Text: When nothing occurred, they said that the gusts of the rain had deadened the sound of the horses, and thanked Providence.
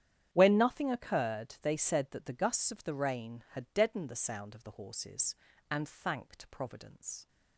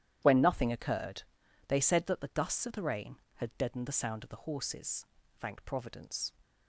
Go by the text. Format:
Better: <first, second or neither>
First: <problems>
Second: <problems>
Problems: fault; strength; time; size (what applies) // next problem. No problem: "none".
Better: first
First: starts louder than the rest; strong; until 1.3 s; 10 dB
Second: starts louder than the rest; strong; until 1.2 s; 11 dB // skips "and"; at 5.2 s